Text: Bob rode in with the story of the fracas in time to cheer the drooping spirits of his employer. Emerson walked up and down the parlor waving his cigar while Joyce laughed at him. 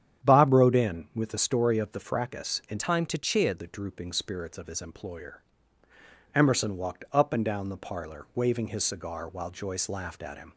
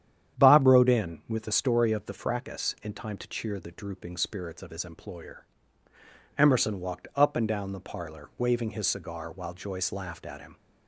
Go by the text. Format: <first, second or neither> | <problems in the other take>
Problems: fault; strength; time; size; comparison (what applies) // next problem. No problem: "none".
second | starts louder than the rest; strong; until 1.3 s; 9 dB; strong in the second // changes voice from "time" to "cheer"; from 2.7 to 3.5 s; 0.8 s long